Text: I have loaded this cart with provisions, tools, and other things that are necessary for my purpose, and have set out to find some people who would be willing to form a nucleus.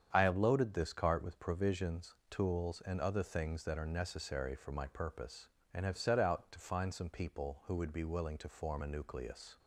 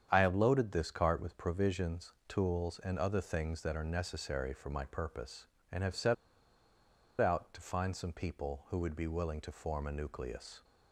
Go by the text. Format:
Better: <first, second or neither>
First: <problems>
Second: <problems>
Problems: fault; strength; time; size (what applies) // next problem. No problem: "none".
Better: first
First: starts louder than the rest; strong; until 1.1 s; 8 dB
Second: starts louder than the rest; strong; until 1.1 s; 8.5 dB // pauses between "set" and "out"; at 6.1 s; 1.0 s long